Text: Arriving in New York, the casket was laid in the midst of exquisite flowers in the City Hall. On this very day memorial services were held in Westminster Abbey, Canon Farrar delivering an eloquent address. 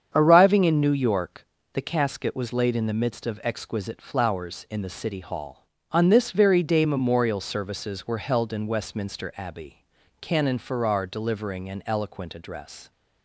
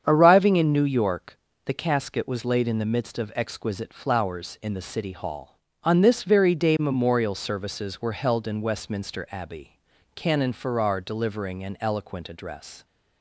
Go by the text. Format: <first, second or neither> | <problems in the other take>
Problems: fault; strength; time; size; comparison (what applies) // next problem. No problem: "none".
neither | starts louder than the rest; strong; the same in both